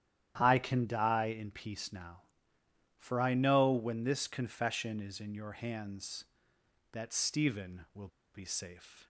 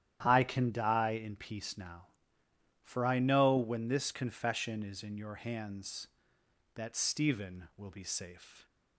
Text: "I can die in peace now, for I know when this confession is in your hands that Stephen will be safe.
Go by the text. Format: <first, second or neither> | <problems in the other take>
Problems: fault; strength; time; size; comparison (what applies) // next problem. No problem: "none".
second | starts louder than the rest; strong; until 1.3 s; 11 dB; strong in the second // pauses between "will" and "be"; slight; at 8.0 s; 0.26 s long